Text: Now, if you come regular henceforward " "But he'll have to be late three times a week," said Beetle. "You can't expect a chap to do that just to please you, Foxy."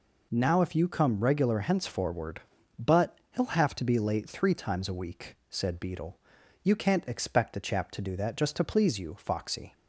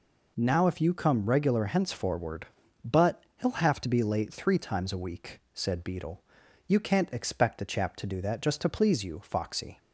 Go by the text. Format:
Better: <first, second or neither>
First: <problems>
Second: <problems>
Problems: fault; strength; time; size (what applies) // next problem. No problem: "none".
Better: neither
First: none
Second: none